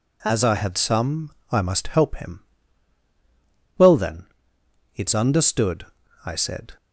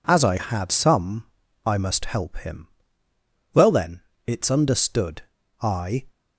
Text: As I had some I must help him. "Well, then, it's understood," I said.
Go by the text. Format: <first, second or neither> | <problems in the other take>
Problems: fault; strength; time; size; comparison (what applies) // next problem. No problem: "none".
first | pauses between "some" and "I"; at 1.2 s; 0.40 s long; slight in the first // stops before "said"; at 6.0 s